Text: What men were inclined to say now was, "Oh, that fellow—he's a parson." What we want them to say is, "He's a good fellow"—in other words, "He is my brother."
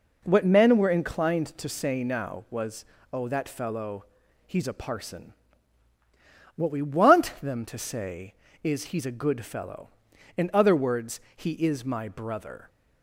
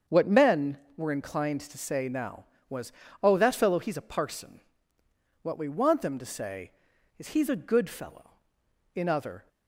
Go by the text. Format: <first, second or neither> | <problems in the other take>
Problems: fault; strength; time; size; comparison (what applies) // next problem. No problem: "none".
first | starts louder than the rest; until 1.2 s; 7 dB // stops before "words He is my brother"; at 9.4 s